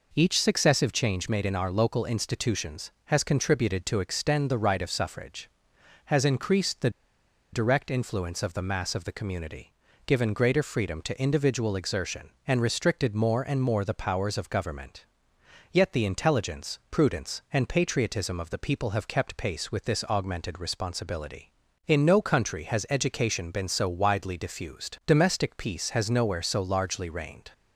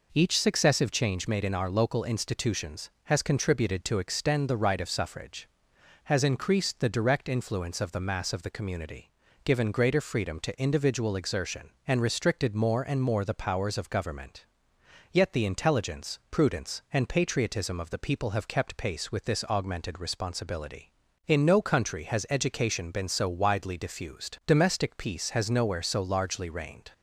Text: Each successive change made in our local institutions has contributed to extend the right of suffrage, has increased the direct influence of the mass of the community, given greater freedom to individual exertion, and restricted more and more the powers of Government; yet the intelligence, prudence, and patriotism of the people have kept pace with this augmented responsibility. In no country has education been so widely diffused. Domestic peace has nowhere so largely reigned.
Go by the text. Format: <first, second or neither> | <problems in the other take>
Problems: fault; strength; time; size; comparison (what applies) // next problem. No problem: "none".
second | pauses between "the" and "direct"; noticeable; at 6.8 s; 0.62 s long